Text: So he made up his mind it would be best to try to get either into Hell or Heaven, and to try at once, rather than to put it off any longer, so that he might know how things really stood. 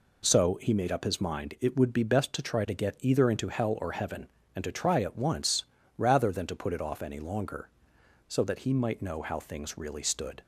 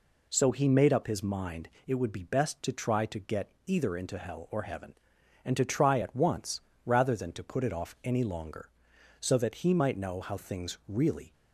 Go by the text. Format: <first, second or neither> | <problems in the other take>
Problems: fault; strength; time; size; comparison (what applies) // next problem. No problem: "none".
first | pauses between "mind" and "it"; slight; at 1.6 s; 0.18 s long // pauses between "get" and "either"; slight; at 3.4 s; 0.16 s long // stops before "stood"; at 11.3 s